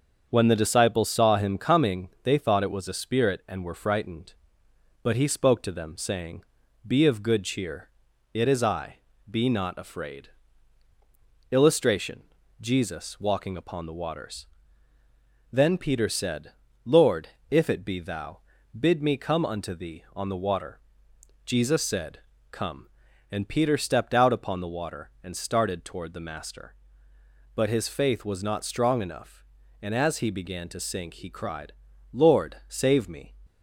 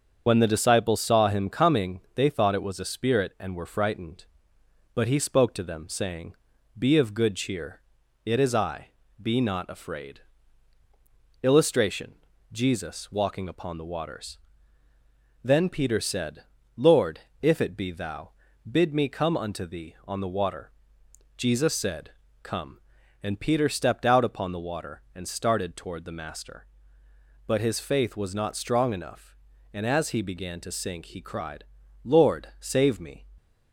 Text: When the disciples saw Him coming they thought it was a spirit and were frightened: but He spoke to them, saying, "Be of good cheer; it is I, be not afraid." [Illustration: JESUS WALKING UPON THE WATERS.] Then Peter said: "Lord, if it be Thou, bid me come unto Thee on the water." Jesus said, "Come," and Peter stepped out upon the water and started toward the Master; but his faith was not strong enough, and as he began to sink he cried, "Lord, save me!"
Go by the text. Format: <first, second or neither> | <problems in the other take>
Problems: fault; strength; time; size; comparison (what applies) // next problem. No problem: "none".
first | loses the start of "When"; at 0.2 s; 50 ms // starts louder than the rest; until 1.2 s; 6.5 dB; also in the first